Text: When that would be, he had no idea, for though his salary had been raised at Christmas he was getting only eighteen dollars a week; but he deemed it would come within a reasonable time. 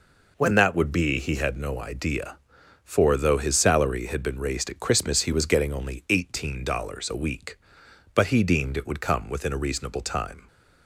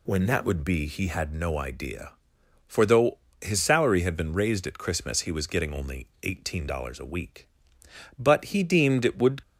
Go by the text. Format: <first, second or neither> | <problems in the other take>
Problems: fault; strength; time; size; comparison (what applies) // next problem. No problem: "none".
first | pauses between "though" and "his"; slight; at 3.1 s; 0.22 s long // pauses between "only" and "eighteen"; slight; at 6.0 s; 0.16 s long // stops before "come within a reasonable time"; at 9.4 s